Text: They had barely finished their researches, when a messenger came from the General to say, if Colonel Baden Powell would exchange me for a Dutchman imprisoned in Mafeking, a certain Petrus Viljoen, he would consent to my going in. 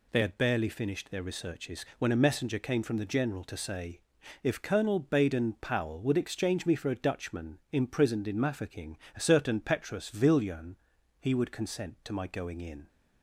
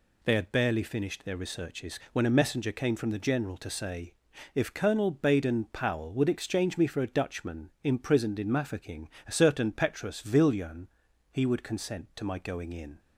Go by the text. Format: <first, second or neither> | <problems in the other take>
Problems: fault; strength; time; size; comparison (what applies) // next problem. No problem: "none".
neither | none